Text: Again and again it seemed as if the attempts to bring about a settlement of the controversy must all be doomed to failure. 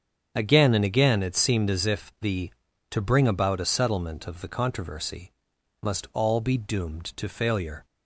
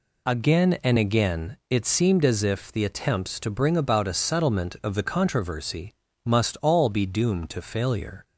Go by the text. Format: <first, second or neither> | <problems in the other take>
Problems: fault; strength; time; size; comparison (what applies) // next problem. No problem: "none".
second | starts louder than the rest; strong; until 1.3 s; 7.5 dB // skips "attempts"; at 2.6 s // pauses between "controversy" and "must"; noticeable; at 5.3 s; 0.50 s long; slight in the second